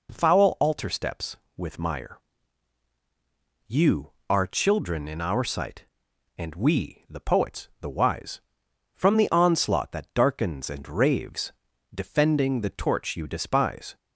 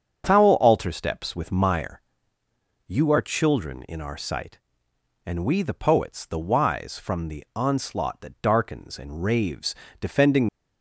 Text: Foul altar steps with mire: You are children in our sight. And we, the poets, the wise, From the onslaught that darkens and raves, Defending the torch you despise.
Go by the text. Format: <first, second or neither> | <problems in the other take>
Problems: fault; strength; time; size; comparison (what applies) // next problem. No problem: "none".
first | starts louder than the rest; strong; until 1.2 s; 7.5 dB // stops before "the torch you despise"; at 10.4 s